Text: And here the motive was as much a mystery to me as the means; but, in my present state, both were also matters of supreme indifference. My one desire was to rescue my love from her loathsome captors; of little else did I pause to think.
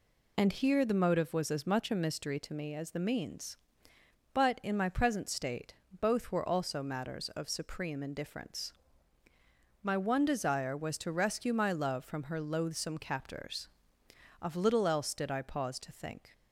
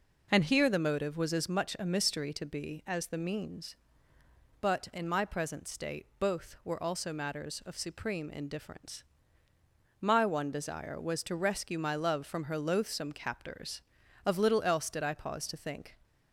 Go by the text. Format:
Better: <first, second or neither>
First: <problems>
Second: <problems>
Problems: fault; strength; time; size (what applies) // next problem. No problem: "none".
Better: first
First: none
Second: says "be" for "me"; at 2.4 s